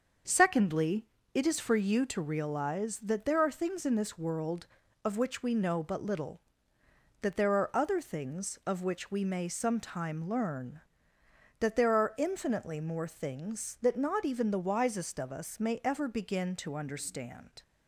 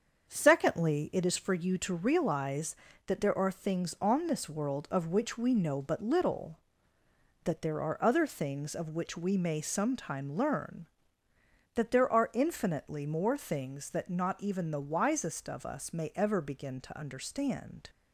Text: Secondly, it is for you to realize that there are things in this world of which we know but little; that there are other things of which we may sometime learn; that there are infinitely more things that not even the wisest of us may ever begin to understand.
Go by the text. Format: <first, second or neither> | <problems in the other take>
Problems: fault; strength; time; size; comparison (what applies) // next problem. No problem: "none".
first | starts louder than the rest; until 1.3 s; 7 dB; also in the first // says "on" for "in"; at 4.0 s